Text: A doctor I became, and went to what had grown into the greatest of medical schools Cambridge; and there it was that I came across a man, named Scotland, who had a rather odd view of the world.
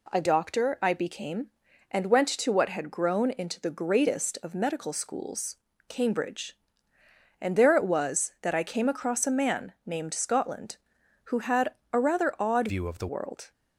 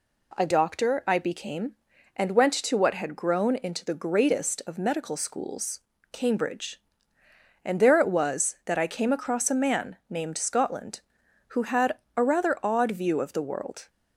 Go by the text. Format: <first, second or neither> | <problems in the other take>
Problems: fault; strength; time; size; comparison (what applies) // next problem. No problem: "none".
second | pauses between "schools" and "Cambridge"; slight; at 5.5 s; 0.32 s long; slight in the second // pauses between "had" and "a"; slight; at 11.7 s; 0.18 s long; slight in the second // changes voice from "view" to "the"; from 12.6 to 13.0 s; 0.4 s long